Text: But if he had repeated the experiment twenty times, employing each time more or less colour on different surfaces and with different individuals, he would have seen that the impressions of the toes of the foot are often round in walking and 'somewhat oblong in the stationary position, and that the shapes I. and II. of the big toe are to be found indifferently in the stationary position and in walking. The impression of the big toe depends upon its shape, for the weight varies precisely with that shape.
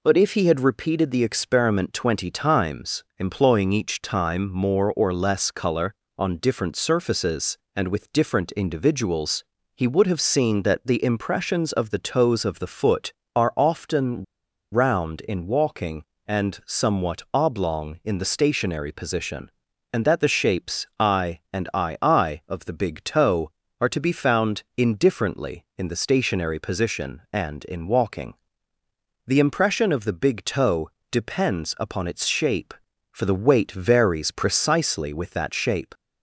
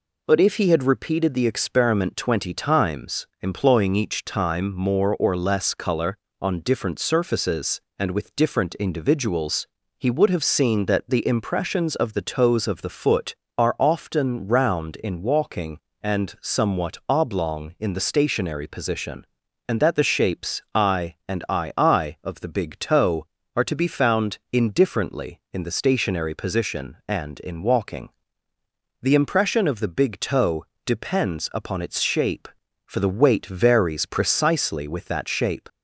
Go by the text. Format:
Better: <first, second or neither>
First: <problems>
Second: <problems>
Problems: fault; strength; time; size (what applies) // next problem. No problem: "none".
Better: second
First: pauses between "often" and "round"; noticeable; at 14.2 s; 0.47 s long // pauses between "toe" and "depends"; slight; at 30.8 s; 0.22 s long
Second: pauses between "toe" and "depends"; slight; at 30.6 s; 0.21 s long